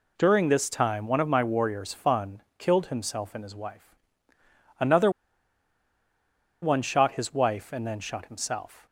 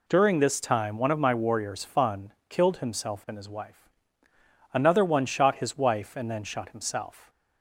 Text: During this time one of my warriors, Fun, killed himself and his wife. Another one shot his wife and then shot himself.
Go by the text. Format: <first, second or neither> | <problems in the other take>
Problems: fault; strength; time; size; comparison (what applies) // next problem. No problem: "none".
second | pauses between "Another" and "one"; strong; at 5.0 s; 1.5 s long